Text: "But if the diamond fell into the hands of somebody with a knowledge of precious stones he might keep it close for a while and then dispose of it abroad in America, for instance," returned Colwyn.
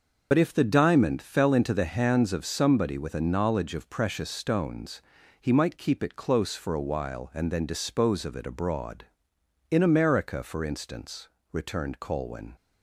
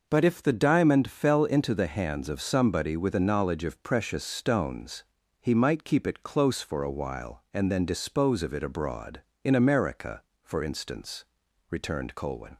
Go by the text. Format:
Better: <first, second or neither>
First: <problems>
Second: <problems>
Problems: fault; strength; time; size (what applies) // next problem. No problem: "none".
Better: second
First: loses the start of "But"; at 0.3 s; 55 ms // pauses between "stones" and "he"; at 5.0 s; 0.38 s long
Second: pauses between "stones" and "he"; slight; at 5.0 s; 0.36 s long